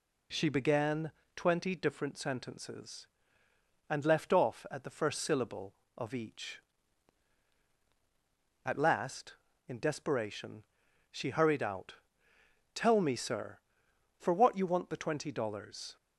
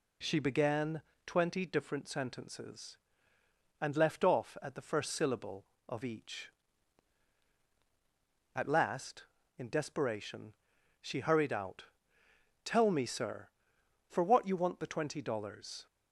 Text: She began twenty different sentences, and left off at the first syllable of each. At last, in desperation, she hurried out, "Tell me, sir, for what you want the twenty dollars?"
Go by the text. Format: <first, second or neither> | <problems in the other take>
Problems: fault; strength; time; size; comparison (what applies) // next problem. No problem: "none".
neither | pauses between "began" and "twenty"; slight; the same in both